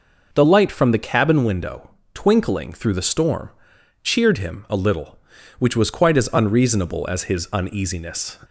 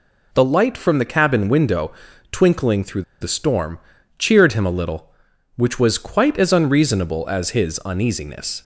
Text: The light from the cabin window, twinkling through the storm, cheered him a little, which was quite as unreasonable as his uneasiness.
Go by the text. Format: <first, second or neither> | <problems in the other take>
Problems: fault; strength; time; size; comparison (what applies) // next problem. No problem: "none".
first | pauses between "through" and "the"; slight; at 3.0 s; 0.18 s long